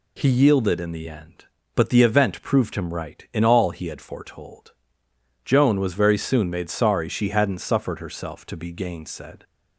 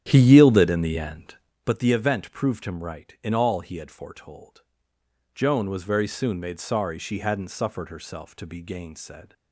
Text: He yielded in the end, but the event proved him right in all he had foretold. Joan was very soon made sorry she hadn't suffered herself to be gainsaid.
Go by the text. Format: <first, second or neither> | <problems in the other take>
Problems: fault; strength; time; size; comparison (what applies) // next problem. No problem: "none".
first | starts louder than the rest; strong; until 1.6 s; 10.5 dB